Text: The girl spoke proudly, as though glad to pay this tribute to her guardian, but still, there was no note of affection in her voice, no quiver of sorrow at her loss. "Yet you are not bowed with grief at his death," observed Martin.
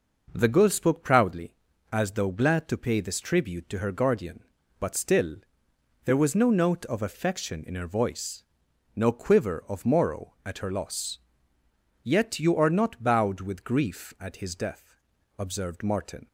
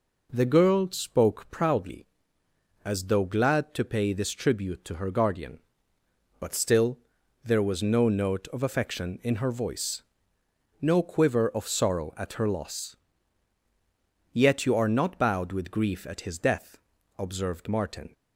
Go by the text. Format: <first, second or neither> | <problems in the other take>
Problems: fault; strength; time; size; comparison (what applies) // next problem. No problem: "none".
second | says "morrow" for "sorrow"; at 9.8 s